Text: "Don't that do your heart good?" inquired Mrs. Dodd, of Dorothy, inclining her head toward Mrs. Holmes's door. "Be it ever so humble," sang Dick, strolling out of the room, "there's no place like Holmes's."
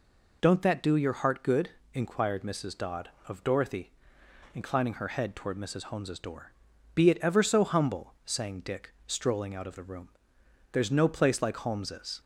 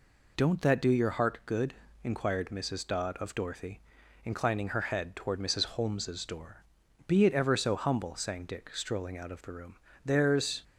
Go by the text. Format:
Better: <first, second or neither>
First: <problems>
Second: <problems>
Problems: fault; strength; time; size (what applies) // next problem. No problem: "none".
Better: first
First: none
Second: stops before "no place like Holmes's"; at 10.6 s